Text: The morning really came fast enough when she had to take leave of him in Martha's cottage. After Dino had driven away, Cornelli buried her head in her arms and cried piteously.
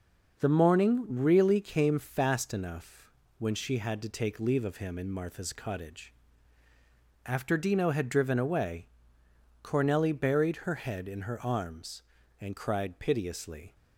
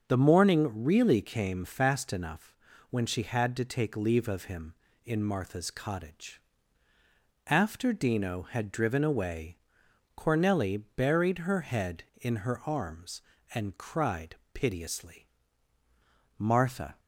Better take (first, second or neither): first